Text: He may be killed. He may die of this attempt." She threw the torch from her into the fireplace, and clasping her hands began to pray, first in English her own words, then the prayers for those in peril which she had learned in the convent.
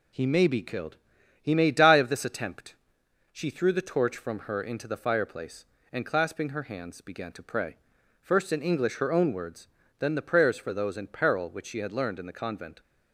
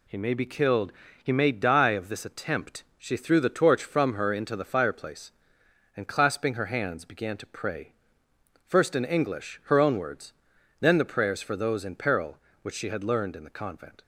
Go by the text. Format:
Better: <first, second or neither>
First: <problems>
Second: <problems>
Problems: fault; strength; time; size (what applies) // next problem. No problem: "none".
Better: neither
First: none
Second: none